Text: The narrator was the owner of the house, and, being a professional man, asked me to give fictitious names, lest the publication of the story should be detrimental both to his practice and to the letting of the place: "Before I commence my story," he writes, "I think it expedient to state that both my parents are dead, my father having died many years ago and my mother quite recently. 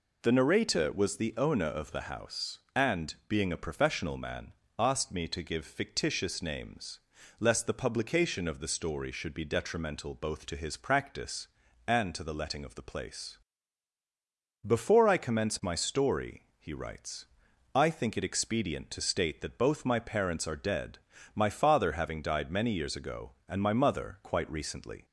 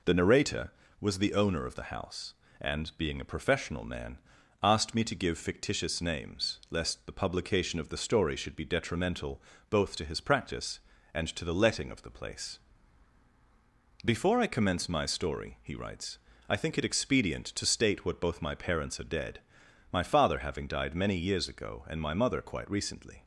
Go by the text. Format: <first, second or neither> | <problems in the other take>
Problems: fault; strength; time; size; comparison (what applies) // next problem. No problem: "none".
first | pauses between "detrimental" and "both"; slight; at 9.4 s; 0.30 s long // says "what" for "that"; at 18.0 s